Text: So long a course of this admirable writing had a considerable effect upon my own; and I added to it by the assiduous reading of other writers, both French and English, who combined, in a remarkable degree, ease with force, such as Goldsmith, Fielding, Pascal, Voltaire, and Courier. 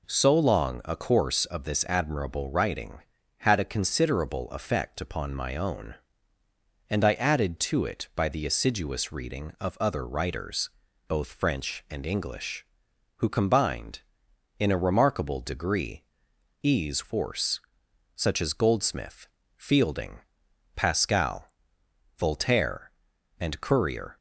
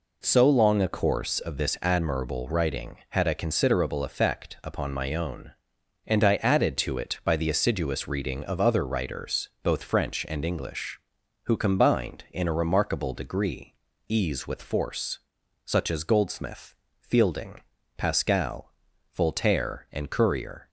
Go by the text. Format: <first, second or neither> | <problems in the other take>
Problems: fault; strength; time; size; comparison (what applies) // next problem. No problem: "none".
second | skips "with"; at 17.0 s